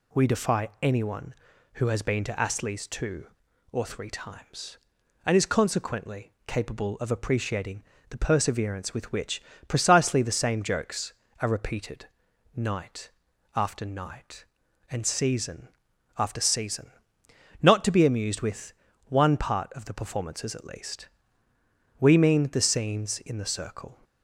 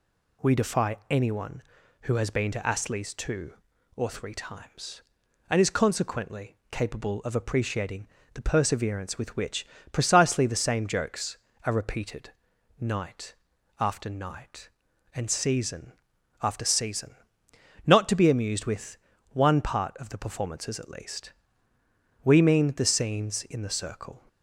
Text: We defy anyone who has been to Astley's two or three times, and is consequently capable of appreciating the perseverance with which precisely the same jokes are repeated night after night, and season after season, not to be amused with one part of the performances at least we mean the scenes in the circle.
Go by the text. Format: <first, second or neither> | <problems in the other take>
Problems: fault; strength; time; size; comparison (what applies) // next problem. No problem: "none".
neither | pauses between "appreciating" and "the"; slight; the same in both // pauses between "which" and "precisely"; slight; the same in both // pauses between "repeated" and "night"; noticeable; the same in both // pauses between "night" and "after"; noticeable; the same in both // pauses between "season" and "after"; noticeable; the same in both // pauses between "with" and "one"; slight; the same in both // pauses between "least" and "we"; noticeable; the same in both